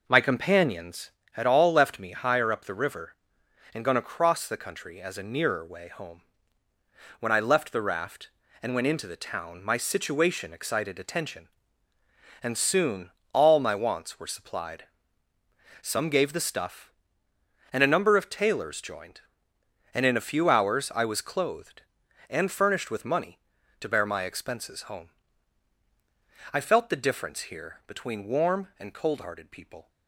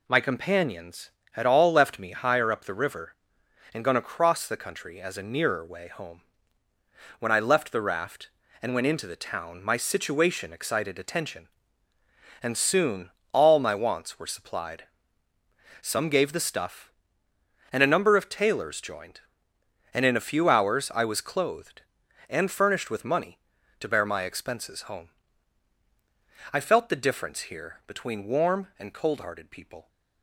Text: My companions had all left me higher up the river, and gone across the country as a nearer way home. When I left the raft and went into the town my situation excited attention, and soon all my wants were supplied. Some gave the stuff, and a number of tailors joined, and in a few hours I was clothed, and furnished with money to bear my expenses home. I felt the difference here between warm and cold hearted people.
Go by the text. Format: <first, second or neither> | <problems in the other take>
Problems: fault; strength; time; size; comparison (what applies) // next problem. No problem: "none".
second | starts louder than the rest; noticeable; until 1.1 s; 5 dB // pauses between "soon" and "all"; slight; at 13.0 s; 0.24 s long; slight in the second